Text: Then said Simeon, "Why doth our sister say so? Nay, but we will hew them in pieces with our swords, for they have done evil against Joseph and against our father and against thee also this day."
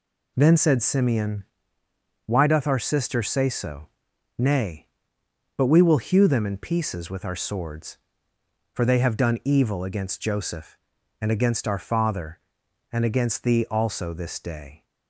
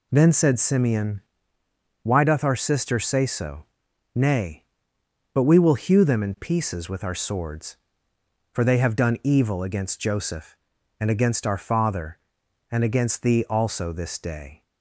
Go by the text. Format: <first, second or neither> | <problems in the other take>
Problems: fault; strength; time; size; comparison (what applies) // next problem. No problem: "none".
neither | none